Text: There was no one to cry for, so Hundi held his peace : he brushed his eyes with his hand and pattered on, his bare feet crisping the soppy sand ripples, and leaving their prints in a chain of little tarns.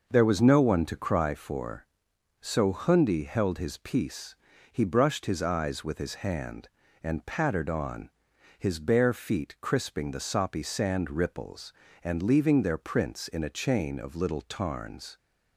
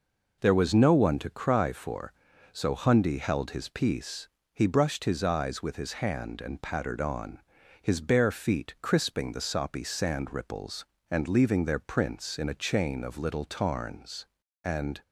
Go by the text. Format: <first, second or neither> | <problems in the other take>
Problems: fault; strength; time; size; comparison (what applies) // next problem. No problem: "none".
first | goes on to say "And"; slight; from 14.6 s on; 0.40 s long